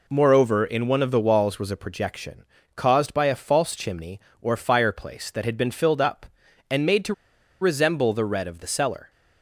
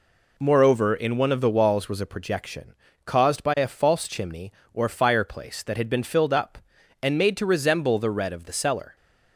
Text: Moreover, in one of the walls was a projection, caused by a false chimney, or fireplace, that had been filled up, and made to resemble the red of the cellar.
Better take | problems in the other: second | pauses between "to" and "resemble"; noticeable; at 7.1 s; 0.48 s long

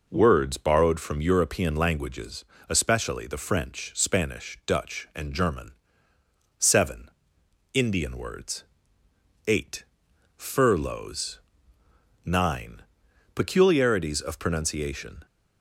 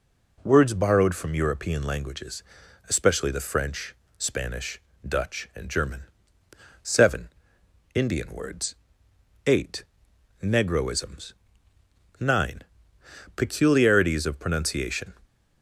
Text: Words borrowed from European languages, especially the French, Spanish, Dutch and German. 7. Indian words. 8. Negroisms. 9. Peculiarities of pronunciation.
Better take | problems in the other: second | says "Furloughs" for "Negroisms"; at 10.3 s

